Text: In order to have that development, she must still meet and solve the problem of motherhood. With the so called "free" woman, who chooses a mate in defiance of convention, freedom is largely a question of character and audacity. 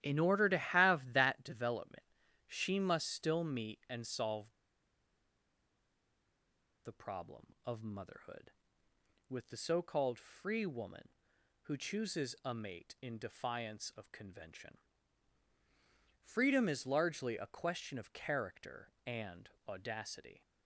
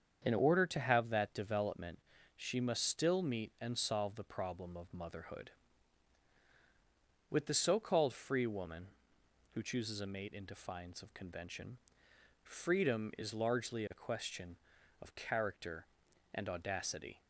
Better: second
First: starts louder than the rest; strong; until 1.0 s; 12 dB // pauses between "solve" and "the"; strong; at 4.5 s; 2.3 s long // pauses between "and" and "audacity"; slight; at 19.4 s; 0.18 s long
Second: starts louder than the rest; strong; until 1.2 s; 7.5 dB

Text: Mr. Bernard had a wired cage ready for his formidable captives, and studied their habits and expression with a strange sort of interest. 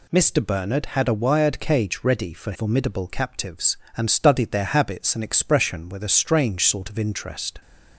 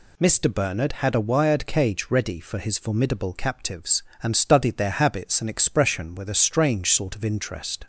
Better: second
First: skips "his"; at 2.5 s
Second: none

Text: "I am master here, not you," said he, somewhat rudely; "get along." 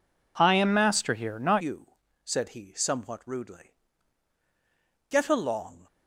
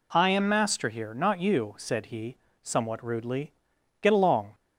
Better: second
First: changes voice at "you"; from 1.5 s on; 4.3 s long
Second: none

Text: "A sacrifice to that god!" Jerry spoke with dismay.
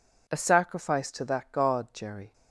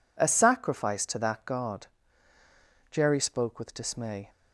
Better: second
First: stops before "spoke with dismay"; at 2.3 s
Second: none

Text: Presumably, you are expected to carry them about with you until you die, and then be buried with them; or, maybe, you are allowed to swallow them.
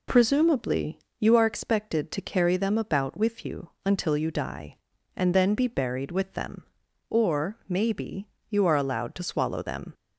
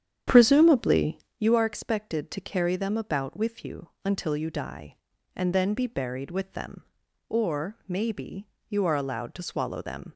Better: first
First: pauses between "you" and "until"; slight; at 3.6 s; 0.16 s long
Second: starts louder than the rest; strong; until 1.4 s; 9 dB // pauses between "you" and "until"; slight; at 3.8 s; 0.16 s long

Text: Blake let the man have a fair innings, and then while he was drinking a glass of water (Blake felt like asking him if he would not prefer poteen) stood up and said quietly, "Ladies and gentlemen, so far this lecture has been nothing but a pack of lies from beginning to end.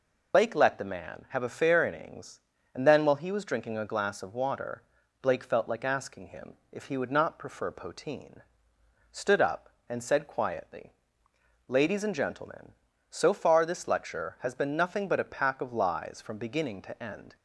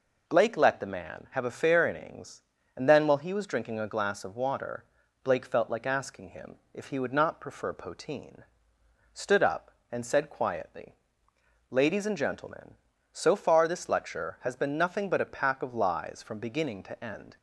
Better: second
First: loses the start of "Blake"; at 0.3 s; 85 ms // pauses between "him" and "if"; slight; at 6.5 s; 0.16 s long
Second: pauses between "him" and "if"; slight; at 6.5 s; 0.16 s long

